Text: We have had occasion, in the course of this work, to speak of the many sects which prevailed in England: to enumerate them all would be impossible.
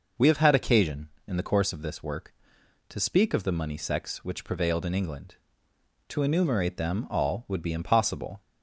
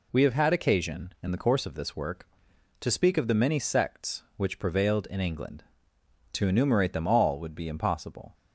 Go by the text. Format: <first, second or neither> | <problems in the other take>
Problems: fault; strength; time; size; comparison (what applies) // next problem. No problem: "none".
second | says "money" for "many"; at 3.5 s